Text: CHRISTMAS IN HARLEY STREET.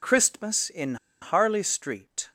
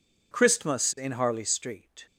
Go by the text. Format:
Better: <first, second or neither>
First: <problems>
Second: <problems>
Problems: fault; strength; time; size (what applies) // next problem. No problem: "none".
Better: second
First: pauses between "IN" and "HARLEY"; slight; at 0.9 s; 0.26 s long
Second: none